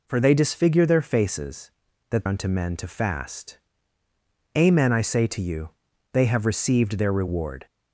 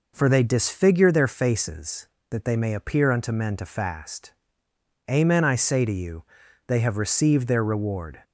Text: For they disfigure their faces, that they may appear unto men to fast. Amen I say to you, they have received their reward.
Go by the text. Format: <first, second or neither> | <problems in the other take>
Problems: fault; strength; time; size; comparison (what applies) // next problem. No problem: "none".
second | skips "they may appear"; at 2.2 s